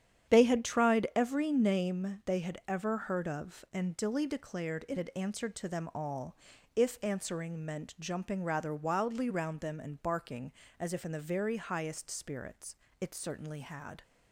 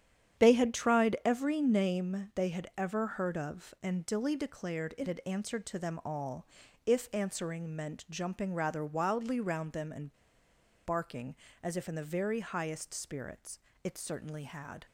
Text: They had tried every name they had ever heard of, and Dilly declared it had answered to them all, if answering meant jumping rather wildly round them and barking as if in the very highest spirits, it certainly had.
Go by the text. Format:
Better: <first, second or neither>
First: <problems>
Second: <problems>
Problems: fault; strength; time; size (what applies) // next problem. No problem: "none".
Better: first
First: starts louder than the rest; strong; until 1.3 s; 9 dB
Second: starts louder than the rest; strong; until 1.4 s; 9 dB // pauses between "and" and "barking"; noticeable; at 10.1 s; 0.72 s long